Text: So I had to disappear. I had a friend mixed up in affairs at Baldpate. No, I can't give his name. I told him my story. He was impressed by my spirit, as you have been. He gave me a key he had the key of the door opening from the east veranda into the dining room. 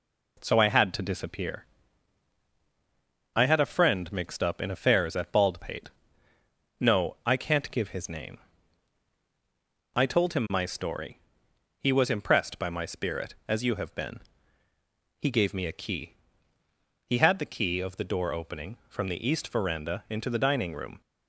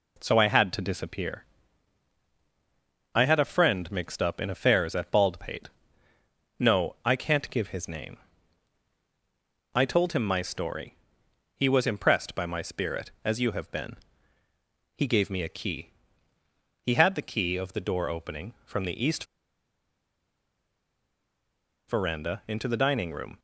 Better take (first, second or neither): first